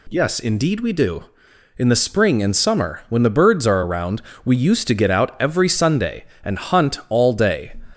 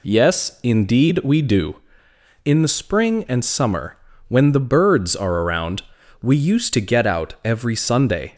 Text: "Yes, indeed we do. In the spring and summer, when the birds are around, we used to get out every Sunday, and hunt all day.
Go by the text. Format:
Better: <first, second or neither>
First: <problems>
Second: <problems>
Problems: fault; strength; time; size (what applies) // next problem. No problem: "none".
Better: first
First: none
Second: stops before "and hunt all day"; at 8.3 s